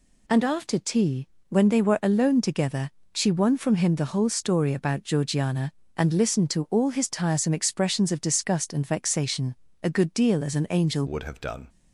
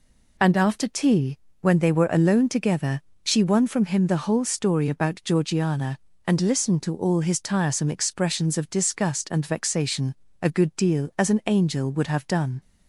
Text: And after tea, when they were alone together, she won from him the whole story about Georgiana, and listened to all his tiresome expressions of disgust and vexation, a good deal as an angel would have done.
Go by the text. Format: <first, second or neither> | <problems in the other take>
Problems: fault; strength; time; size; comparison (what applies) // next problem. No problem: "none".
second | changes voice at "would"; from 11.0 s on; 0.6 s long